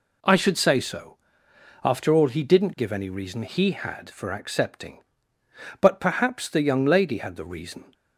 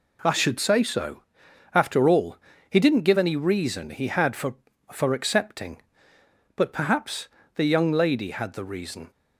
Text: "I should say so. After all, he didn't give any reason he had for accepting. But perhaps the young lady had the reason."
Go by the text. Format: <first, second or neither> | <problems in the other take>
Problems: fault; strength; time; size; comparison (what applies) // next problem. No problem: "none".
first | says "for" twice; at 4.9 s // pauses between "perhaps" and "the"; slight; at 7.2 s; 0.26 s long